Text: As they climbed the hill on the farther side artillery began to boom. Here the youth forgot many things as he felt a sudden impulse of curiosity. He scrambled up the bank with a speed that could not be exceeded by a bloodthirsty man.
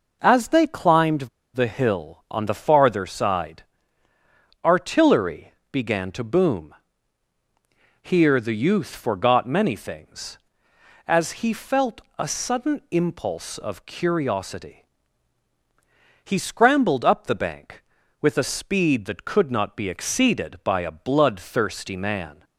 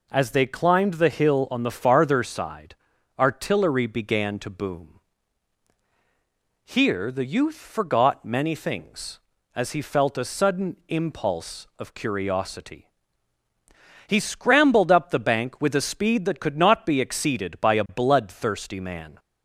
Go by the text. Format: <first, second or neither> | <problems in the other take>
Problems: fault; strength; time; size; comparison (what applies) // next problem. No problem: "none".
second | pauses between "climbed" and "the"; slight; at 1.2 s; 0.26 s long // pauses between "side" and "artillery"; at 3.6 s; 1.0 s long; also in the second // pauses between "artillery" and "began"; slight; at 5.5 s; 0.20 s long // pauses between "felt" and "a"; slight; at 11.9 s; 0.18 s long